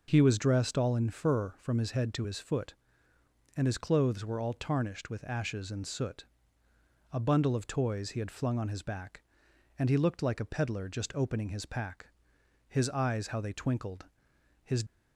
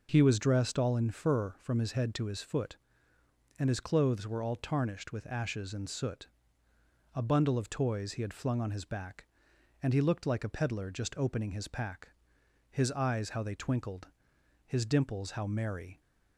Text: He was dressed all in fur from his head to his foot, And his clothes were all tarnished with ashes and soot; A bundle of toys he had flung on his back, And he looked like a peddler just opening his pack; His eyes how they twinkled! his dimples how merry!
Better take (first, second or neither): second